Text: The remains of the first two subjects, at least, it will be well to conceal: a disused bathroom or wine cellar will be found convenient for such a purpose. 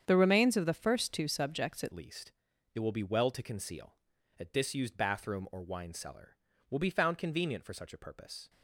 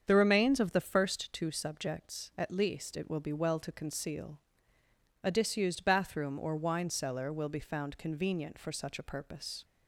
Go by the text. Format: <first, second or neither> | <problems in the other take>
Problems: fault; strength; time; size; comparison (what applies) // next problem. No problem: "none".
second | starts louder than the rest; strong; until 1.0 s; 8 dB; strong in the second // changes voice at "least"; from 1.9 s on; 6.5 s long